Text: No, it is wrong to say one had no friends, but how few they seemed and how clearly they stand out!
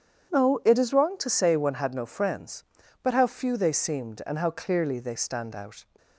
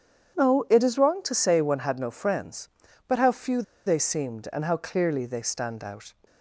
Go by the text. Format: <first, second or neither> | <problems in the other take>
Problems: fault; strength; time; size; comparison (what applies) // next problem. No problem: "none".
first | starts louder than the rest; strong; until 1.4 s; 8.5 dB; strong in the first // pauses between "few" and "they"; slight; at 3.6 s; 0.24 s long